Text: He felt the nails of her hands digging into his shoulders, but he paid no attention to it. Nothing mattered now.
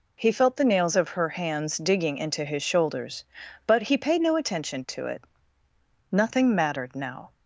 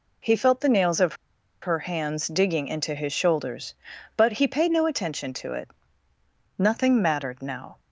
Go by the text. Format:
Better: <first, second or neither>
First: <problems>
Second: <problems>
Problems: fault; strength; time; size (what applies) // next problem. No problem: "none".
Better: first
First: none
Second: pauses between "of" and "her"; noticeable; at 1.1 s; 0.46 s long